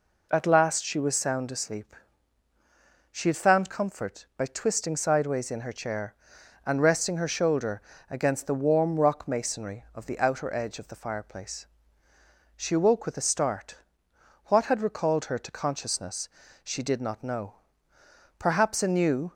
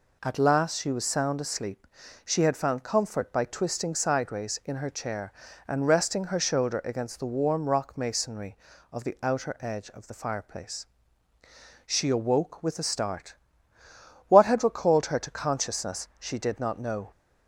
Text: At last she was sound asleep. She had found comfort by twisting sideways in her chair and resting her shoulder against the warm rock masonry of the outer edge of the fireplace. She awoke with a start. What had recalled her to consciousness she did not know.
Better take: second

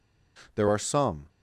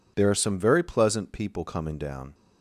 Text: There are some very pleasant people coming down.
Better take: second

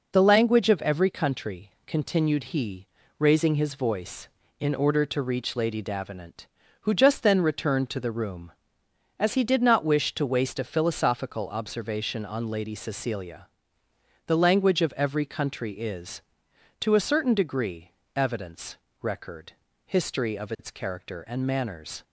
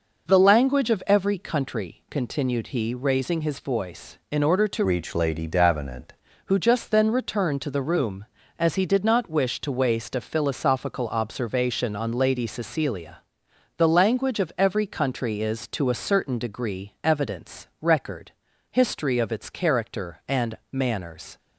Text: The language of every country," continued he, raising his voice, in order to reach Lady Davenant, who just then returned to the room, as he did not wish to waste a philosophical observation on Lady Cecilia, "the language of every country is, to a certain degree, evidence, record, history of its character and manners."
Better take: first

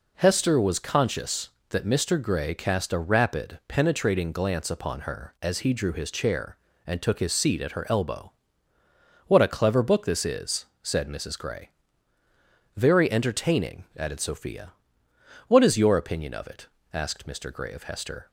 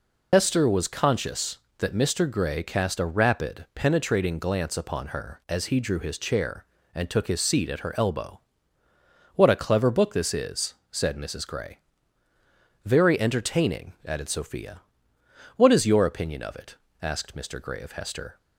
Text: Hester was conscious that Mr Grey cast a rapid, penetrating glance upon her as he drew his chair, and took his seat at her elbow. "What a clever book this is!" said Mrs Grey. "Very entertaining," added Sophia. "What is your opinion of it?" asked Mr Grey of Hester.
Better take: first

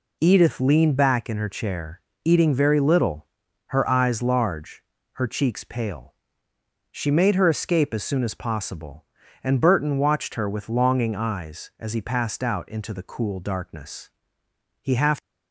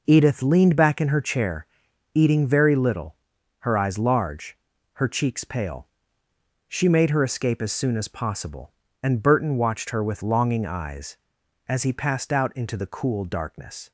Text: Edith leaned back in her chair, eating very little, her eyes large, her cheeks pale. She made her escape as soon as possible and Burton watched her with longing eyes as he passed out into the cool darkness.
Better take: second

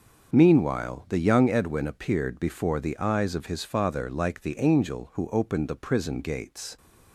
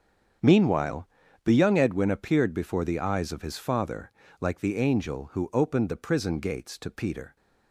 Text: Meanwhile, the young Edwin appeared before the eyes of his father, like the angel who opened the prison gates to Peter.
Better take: second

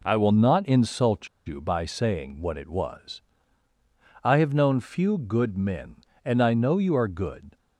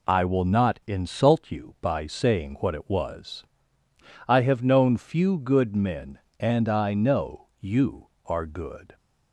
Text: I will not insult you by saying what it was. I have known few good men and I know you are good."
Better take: second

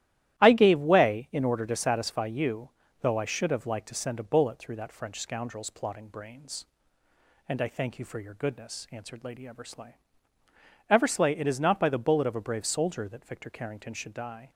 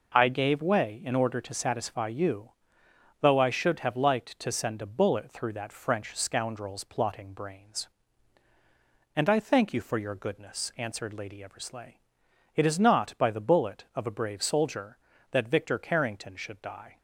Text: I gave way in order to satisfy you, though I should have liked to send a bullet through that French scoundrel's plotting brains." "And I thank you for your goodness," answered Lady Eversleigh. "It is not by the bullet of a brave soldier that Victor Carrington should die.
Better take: second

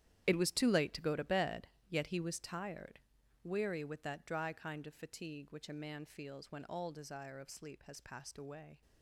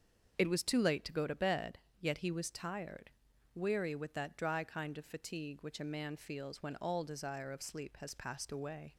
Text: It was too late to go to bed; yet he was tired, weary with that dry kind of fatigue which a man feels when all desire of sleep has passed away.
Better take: second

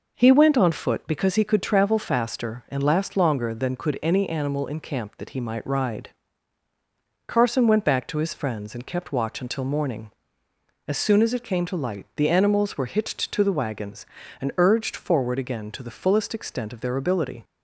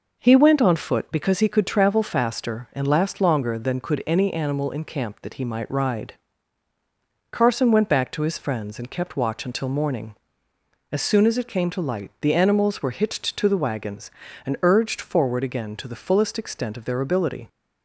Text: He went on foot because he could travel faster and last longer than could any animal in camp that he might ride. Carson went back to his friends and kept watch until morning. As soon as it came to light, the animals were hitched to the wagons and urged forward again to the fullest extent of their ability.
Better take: neither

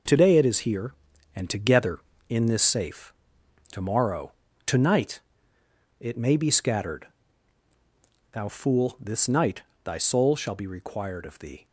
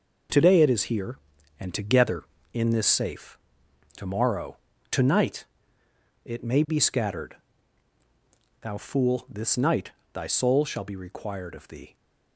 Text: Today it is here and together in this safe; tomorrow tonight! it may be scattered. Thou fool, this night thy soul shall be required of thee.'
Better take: neither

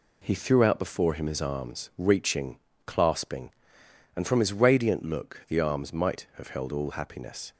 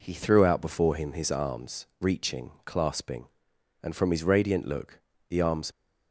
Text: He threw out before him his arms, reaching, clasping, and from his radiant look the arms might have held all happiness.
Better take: first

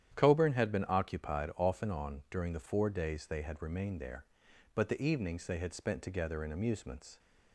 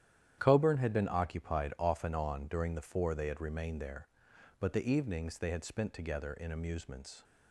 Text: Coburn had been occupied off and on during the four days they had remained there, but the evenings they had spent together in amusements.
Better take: first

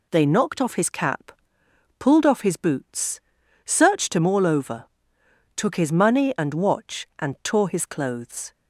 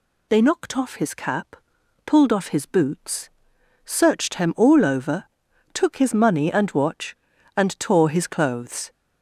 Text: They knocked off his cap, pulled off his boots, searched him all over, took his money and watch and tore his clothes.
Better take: neither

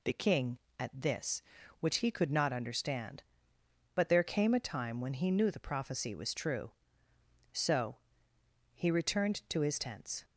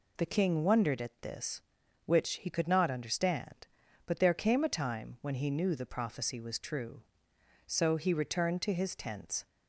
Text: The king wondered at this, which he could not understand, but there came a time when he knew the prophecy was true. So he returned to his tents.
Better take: second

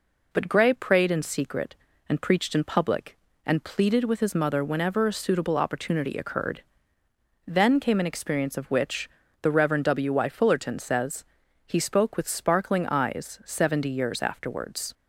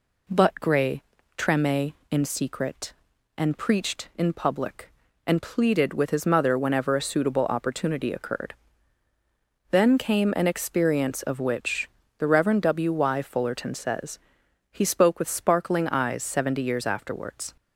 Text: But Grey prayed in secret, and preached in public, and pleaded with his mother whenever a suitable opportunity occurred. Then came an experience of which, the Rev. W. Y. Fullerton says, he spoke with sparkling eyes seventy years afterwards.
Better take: first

